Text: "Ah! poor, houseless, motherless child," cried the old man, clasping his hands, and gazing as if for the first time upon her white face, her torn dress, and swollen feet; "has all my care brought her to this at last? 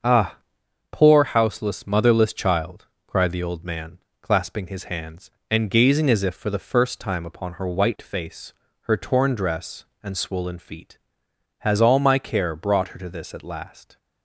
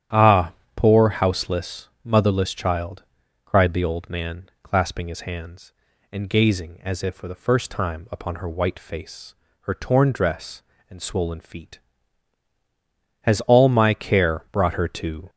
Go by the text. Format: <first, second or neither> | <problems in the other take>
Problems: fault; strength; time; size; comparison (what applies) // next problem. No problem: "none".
first | starts louder than the rest; strong; until 1.3 s; 10.5 dB; also in the first // stops before "this at last"; at 15.2 s